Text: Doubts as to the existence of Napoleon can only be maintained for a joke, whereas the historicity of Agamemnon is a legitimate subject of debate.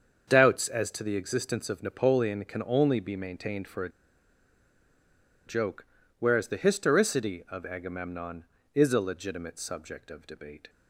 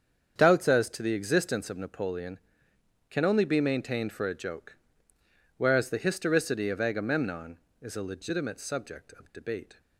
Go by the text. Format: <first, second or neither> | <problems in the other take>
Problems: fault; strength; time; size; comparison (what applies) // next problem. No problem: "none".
second | starts louder than the rest; until 1.2 s; 7 dB; strong in the second // pauses between "a" and "joke"; strong; at 3.8 s; 1.5 s long